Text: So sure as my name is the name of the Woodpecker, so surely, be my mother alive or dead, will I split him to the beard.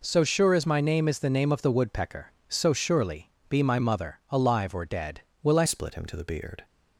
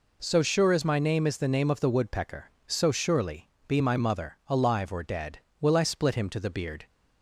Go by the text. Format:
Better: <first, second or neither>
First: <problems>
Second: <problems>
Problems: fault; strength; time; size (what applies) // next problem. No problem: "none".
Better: second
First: changes voice at "split"; from 5.6 s on; 1.0 s long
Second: none